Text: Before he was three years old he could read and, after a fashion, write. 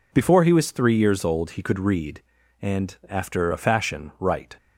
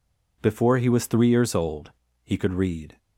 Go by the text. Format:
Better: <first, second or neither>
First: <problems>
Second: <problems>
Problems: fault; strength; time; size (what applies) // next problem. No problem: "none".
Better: first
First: none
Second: pauses between "old" and "he"; slight; at 1.9 s; 0.32 s long // stops before "and after a fashion write"; at 2.9 s